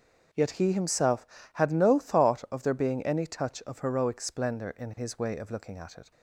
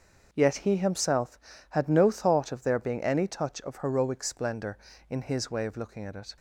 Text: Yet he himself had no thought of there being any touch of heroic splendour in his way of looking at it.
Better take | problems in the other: neither | starts louder than the rest; the same in both

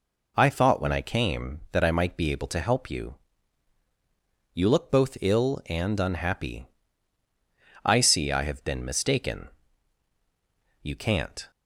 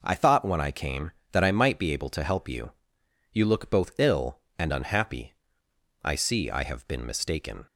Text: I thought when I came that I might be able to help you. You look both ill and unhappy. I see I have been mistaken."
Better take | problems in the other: second | goes on to say "You can't"; noticeable; from 10.8 s on; 0.68 s long

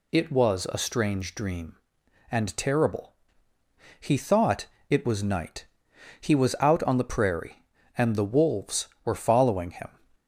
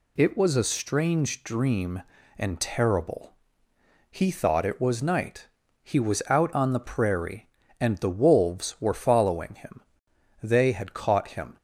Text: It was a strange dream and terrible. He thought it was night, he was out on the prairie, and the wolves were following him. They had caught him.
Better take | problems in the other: second | pauses between "thought" and "it"; slight; at 4.6 s; 0.22 s long // stops before "They had caught him"; at 10.1 s

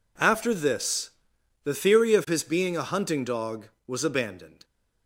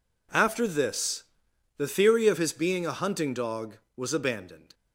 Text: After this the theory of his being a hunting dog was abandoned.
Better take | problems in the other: neither | pauses between "this" and "the"; noticeable; the same in both

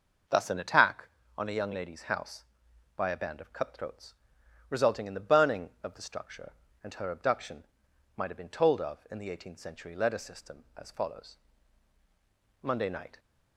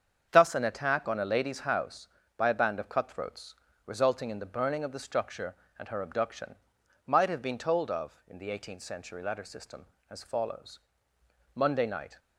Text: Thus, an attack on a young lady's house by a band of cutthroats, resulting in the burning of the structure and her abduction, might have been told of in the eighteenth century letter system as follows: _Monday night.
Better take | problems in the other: first | starts louder than the rest; strong; until 1.3 s; 7.5 dB // skips "young"; at 1.2 s

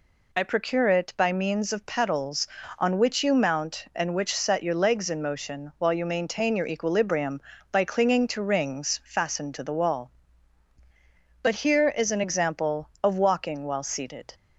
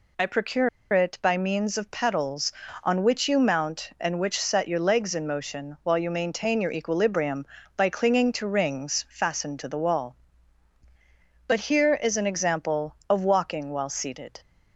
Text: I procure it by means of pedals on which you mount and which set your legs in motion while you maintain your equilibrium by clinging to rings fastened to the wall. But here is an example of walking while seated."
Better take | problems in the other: first | pauses between "procure" and "it"; slight; at 0.6 s; 0.23 s long

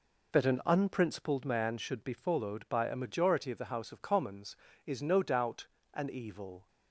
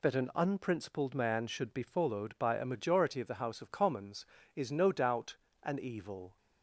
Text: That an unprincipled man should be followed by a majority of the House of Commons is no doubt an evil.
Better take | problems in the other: second | starts louder than the rest; noticeable; until 1.4 s; 4 dB // pauses between "doubt" and "an"; slight; at 5.6 s; 0.26 s long; slight in the second

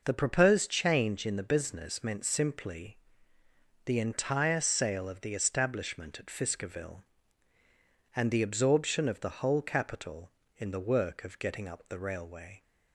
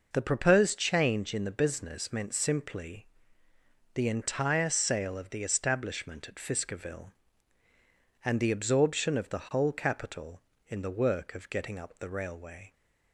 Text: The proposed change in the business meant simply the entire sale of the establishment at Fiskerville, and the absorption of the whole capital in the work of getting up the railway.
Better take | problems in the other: neither | pauses between "simply" and "the"; noticeable; the same in both

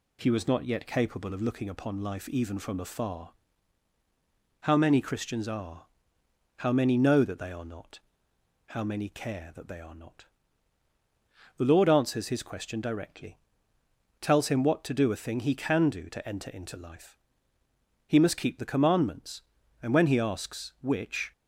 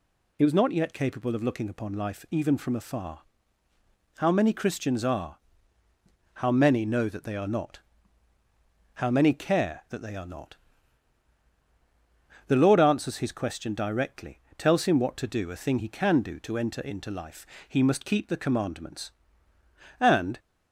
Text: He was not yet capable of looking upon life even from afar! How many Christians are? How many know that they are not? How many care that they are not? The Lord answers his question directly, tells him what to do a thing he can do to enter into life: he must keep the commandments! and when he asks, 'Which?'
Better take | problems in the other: first | stops before "when he asks Which"; at 20.3 s

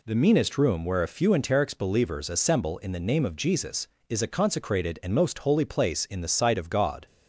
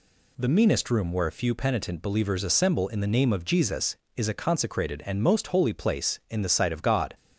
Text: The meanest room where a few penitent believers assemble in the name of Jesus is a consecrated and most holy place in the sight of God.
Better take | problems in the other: second | says "enterics" for "penitent"; at 1.2 s

